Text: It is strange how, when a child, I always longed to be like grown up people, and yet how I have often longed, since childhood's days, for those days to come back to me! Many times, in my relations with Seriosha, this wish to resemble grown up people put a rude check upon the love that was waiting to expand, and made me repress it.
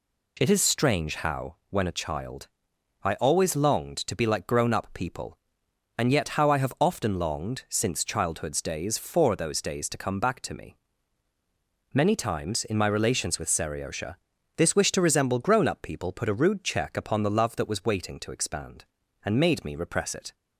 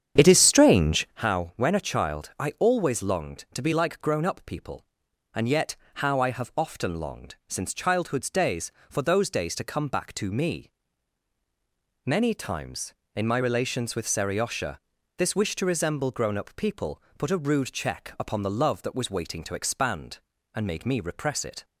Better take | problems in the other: first | starts louder than the rest; strong; until 1.2 s; 8.5 dB // pauses between "yet" and "how"; slight; at 5.7 s; 0.20 s long // pauses between "people" and "put"; slight; at 17.0 s; 0.16 s long

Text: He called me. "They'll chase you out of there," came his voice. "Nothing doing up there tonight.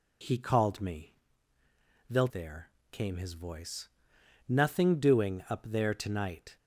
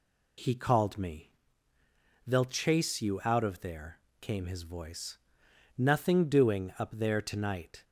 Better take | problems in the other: second | skips "chase you out of"; at 2.2 s

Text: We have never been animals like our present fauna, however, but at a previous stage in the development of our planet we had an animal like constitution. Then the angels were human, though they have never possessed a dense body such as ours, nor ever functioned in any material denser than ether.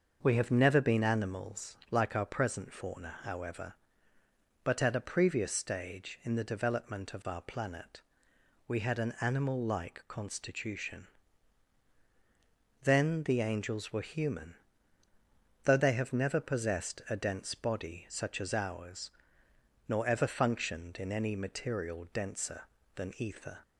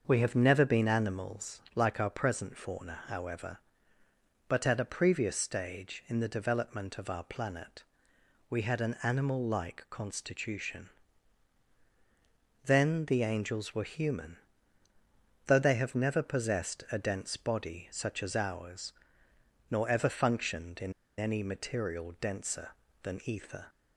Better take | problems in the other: first | starts louder than the rest; until 1.0 s; 6.5 dB; also in the first // pauses between "planet" and "we"; noticeable; at 7.8 s; 0.66 s long; noticeable in the first // pauses between "in" and "any"; slight; at 20.9 s; 0.26 s long

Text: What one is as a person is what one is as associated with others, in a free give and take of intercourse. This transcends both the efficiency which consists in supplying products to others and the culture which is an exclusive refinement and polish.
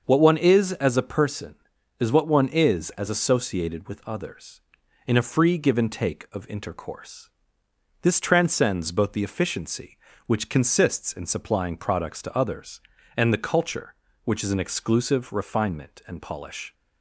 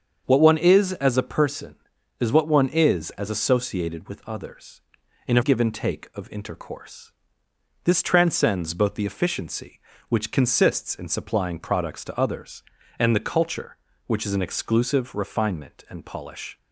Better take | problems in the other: first | starts louder than the rest; until 1.2 s; 7 dB; also in the first // skips "free"; at 5.4 s

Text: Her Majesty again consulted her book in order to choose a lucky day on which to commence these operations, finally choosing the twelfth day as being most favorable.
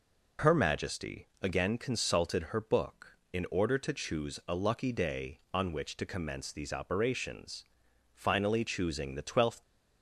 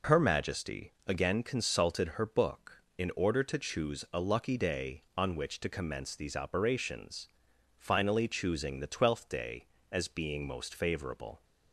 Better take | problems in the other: second | pauses between "Majesty" and "again"; slight; at 1.2 s; 0.16 s long; slight in the second // stops before "day as being most favorable"; at 9.6 s

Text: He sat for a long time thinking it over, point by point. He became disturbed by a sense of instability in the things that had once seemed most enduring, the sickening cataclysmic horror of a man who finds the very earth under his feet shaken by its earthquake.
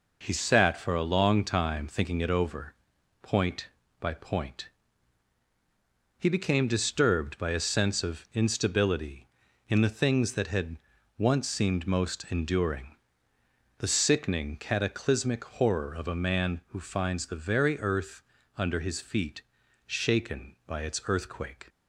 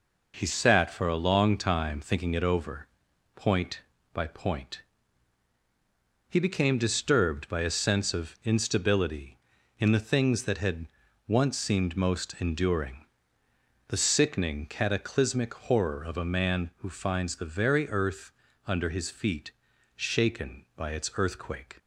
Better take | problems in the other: neither | pauses between "had" and "once"; the same in both // pauses between "earth" and "under"; slight; the same in both // pauses between "feet" and "shaken"; the same in both

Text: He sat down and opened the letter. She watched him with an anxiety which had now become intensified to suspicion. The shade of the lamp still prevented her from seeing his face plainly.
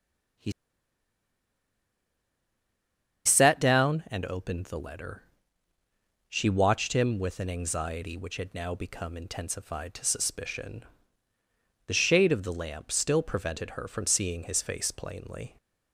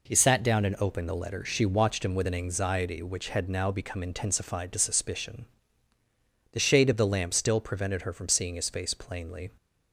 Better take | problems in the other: second | starts louder than the rest; strong; until 4.1 s; 8 dB // pauses between "He" and "sat"; strong; at 0.5 s; 2.7 s long

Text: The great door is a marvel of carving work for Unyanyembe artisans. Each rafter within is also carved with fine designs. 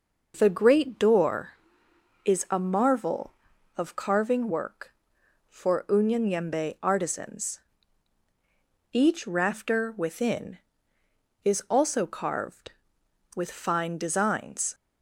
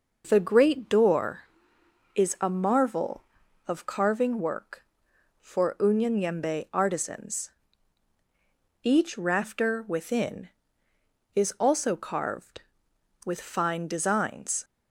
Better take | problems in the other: neither | none

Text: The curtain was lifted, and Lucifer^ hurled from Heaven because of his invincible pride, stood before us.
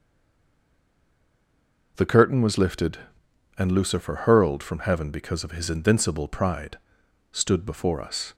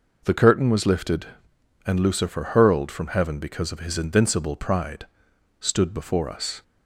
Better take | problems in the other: second | stays silent before the first word; noticeable; until 1.9 s; 1.9 s long

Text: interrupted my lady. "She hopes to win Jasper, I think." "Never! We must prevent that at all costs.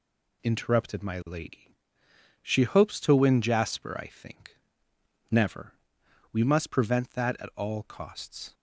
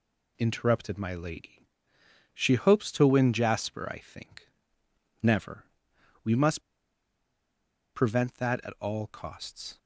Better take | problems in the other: first | pauses between "must" and "prevent"; strong; at 6.6 s; 1.3 s long

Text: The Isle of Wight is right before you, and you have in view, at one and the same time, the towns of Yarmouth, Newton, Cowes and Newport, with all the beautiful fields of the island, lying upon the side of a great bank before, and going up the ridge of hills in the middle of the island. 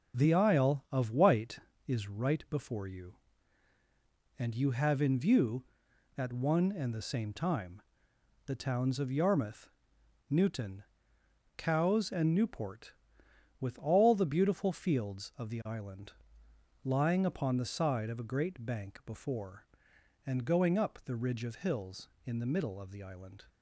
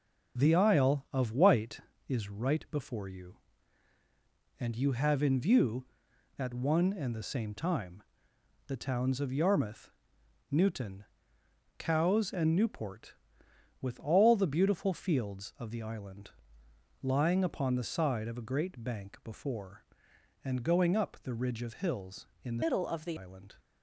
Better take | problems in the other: first | starts louder than the rest; until 1.4 s; 6.5 dB; also in the first // changes voice from "middle" to "the"; from 22.6 to 23.1 s; 0.5 s long

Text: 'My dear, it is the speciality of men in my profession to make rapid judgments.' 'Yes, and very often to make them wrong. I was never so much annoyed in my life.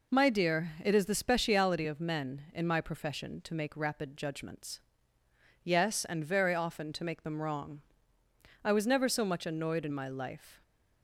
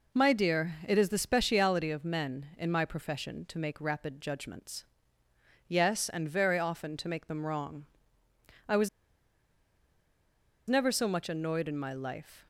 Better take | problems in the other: first | pauses between "was" and "never"; strong; at 8.8 s; 1.8 s long

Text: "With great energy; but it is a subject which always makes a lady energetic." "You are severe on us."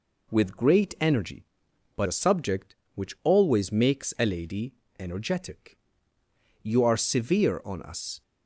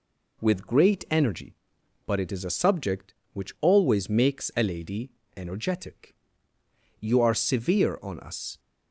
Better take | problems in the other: second | skips "it is"; at 2.0 s // pauses between "lady" and "energetic"; slight; at 4.7 s; 0.26 s long; slight in the second

